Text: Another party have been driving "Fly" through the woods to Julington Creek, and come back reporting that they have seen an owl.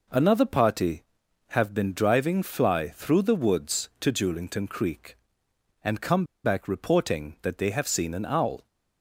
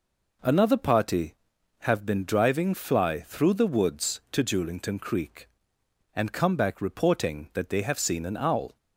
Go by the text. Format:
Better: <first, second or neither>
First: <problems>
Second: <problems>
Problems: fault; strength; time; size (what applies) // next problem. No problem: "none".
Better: second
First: pauses between "come" and "back"; slight; at 6.2 s; 0.20 s long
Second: none